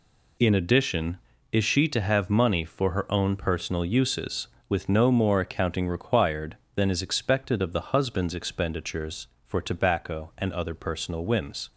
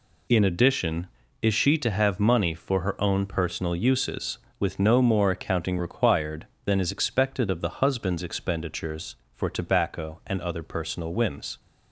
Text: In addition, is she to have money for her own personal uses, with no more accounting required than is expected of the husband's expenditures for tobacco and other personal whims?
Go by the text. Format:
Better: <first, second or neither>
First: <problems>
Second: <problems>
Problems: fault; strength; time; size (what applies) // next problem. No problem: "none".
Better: neither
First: none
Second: none